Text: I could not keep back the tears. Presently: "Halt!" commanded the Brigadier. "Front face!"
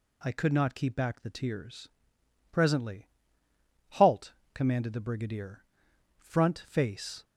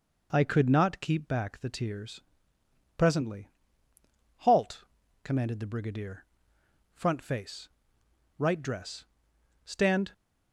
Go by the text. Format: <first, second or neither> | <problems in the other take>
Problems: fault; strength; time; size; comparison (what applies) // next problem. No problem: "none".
first | goes on to say "Right dress Stand"; strong; from 8.3 s on; 1.7 s long